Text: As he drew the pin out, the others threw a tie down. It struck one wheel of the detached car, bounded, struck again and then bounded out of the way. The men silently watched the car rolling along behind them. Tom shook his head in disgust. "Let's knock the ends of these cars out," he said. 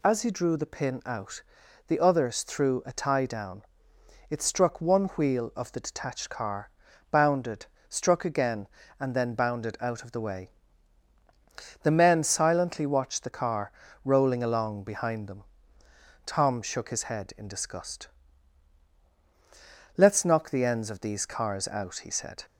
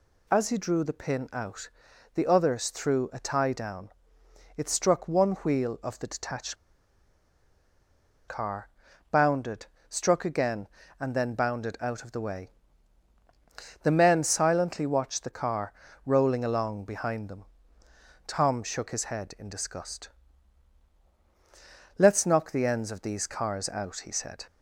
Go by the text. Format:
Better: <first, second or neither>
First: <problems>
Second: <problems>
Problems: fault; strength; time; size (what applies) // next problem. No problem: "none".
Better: first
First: pauses between "car" and "rolling"; slight; at 13.7 s; 0.32 s long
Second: pauses between "detached" and "car"; strong; at 6.5 s; 1.7 s long // pauses between "car" and "rolling"; slight; at 15.7 s; 0.32 s long